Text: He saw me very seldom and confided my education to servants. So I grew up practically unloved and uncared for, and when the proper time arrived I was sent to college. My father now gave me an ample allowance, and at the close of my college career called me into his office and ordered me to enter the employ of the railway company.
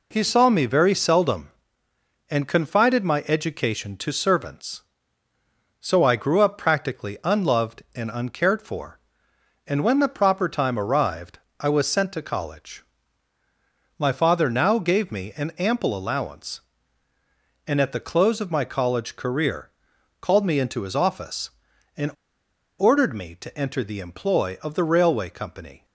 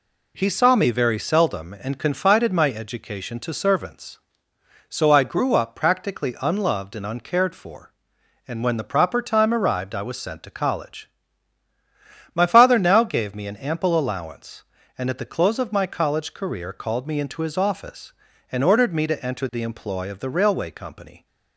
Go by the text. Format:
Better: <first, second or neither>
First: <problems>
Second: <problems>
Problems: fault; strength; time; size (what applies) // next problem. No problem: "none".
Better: second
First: pauses between "arrived" and "I"; slight; at 11.3 s; 0.24 s long // pauses between "career" and "called"; noticeable; at 19.6 s; 0.50 s long // pauses between "and" and "ordered"; noticeable; at 22.1 s; 0.67 s long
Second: none